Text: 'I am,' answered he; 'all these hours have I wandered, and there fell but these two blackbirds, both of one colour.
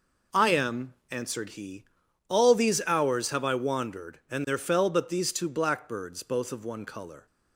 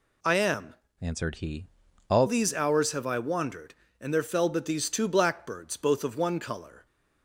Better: first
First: none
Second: changes voice from "answered" to "all"; from 0.9 to 2.2 s; 1.3 s long

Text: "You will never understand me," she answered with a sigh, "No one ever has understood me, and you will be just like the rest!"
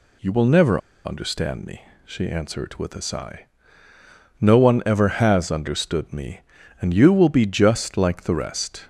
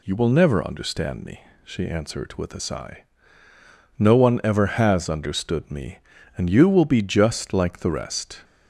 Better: second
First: pauses between "never" and "understand"; slight; at 0.8 s; 0.27 s long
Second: none

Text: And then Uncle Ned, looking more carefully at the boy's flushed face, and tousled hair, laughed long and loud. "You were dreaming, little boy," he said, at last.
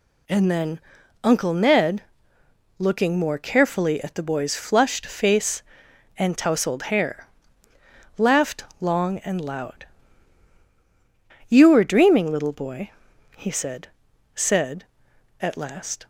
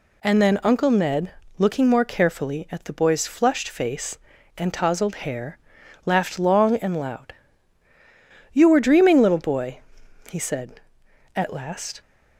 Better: second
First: pauses between "then" and "Uncle"; at 0.7 s; 0.44 s long // pauses between "laughed" and "long"; slight; at 8.6 s; 0.16 s long // says "said" twice; at 14.3 s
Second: none

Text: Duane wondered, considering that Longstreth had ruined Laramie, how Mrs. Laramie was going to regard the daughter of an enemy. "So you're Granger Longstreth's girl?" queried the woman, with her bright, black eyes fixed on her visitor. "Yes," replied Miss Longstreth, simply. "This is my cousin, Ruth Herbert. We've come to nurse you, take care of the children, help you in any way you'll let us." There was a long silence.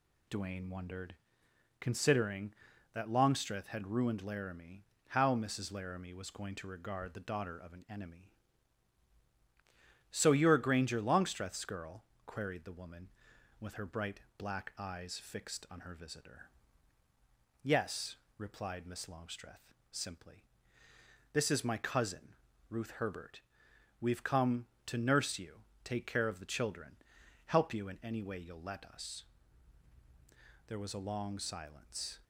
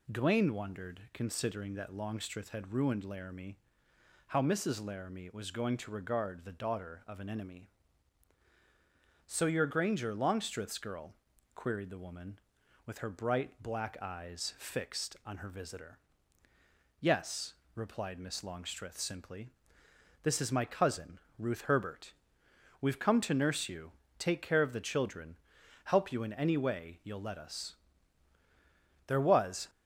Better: first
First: none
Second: stops before "a long silence"; at 29.6 s

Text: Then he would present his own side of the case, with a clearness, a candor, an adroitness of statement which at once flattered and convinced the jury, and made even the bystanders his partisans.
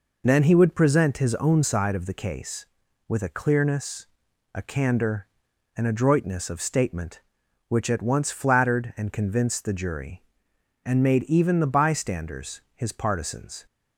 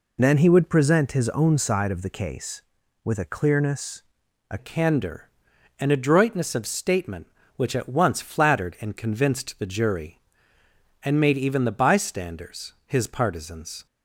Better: first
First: none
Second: changes voice at "candor"; from 4.5 s on; 9.3 s long

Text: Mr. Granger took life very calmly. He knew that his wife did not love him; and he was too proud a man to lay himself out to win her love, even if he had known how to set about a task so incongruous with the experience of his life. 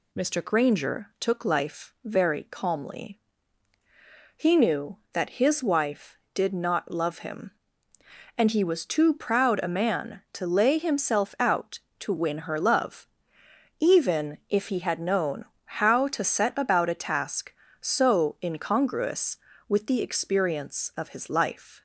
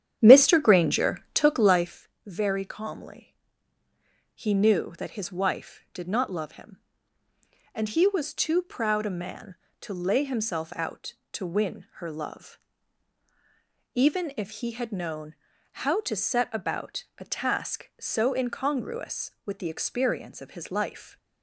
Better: first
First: pauses between "known" and "how"; slight; at 15.4 s; 0.34 s long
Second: starts louder than the rest; strong; until 2.0 s; 9.5 dB // pauses between "Granger" and "took"; slight; at 1.1 s; 0.16 s long // pauses between "life" and "very"; slight; at 2.0 s; 0.18 s long // pauses between "known" and "how"; noticeable; at 15.3 s; 0.48 s long // pauses between "about" and "a"; slight; at 17.0 s; 0.16 s long

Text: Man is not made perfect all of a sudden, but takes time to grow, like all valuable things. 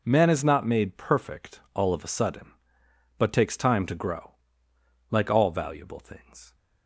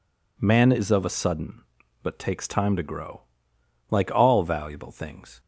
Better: first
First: none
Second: skips "not made perfect all"; at 0.9 s

